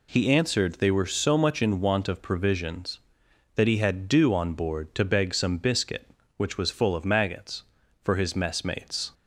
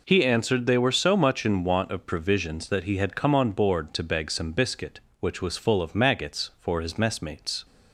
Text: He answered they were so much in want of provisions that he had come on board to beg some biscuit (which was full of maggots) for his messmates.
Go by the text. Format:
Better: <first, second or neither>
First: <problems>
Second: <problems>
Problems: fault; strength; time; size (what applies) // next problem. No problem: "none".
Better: second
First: says "dew" for "come"; at 4.0 s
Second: none